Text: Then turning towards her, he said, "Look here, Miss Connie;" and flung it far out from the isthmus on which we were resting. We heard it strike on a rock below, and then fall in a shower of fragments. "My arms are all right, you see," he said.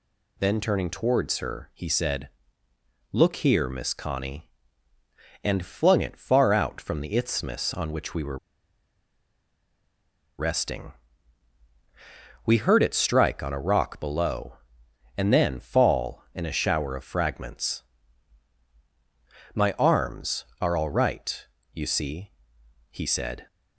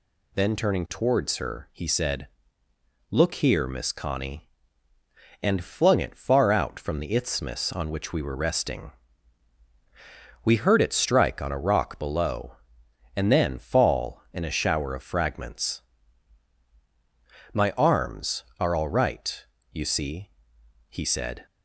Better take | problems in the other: second | pauses between "were" and "resting"; strong; at 8.3 s; 2.0 s long

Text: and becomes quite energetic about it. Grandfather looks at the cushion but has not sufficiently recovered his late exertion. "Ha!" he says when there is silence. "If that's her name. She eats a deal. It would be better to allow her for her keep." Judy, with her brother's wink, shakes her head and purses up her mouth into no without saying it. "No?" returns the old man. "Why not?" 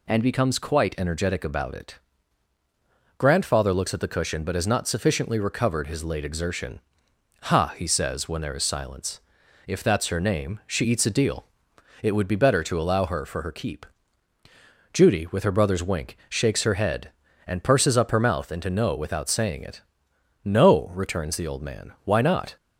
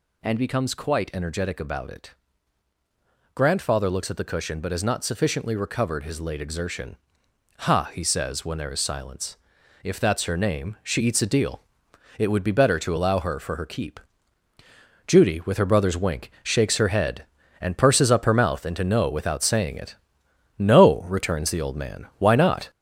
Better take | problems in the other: first | gets louder; noticeable; throughout; 5 dB

